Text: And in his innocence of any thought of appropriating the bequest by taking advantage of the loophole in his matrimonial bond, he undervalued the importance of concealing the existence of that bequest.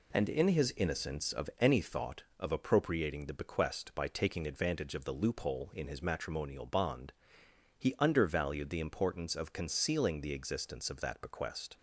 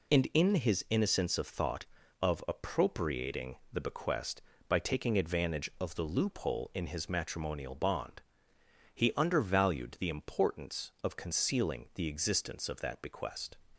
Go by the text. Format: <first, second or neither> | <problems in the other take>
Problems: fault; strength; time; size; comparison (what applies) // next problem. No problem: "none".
first | skips "any"; at 1.4 s // pauses between "appropriating" and "the"; slight; at 3.5 s; 0.16 s long